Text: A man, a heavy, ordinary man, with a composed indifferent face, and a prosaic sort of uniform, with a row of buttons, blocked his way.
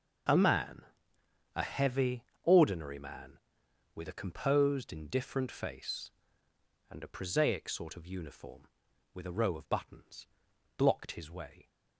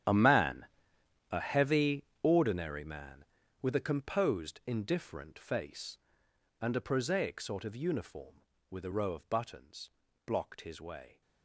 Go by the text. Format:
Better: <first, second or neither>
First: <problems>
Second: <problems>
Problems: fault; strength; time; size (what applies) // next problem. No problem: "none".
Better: first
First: starts louder than the rest; noticeable; until 2.0 s; 6 dB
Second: gets quieter; strong; throughout; 17.5 dB // starts louder than the rest; strong; until 1.7 s; 10.5 dB